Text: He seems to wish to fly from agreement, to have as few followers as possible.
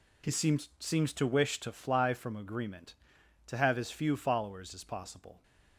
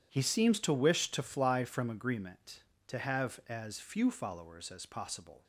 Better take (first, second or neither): second